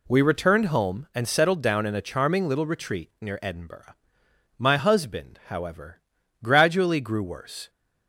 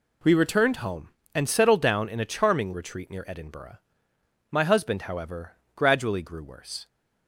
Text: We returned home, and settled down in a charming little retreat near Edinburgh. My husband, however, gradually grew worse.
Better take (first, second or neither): first